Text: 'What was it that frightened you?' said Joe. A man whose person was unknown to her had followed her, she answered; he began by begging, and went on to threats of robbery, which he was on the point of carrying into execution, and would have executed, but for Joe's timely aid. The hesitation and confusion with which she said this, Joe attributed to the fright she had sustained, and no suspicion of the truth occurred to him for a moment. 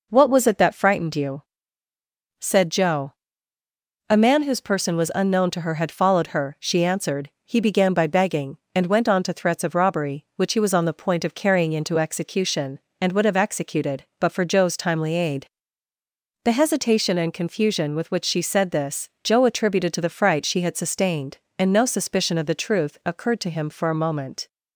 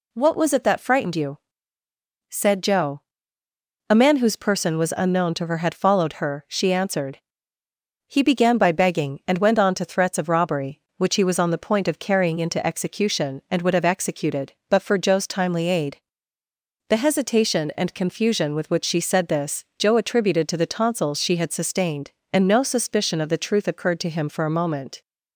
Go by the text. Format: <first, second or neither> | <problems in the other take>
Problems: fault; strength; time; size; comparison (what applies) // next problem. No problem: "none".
first | says "tonsils" for "fright"; at 20.6 s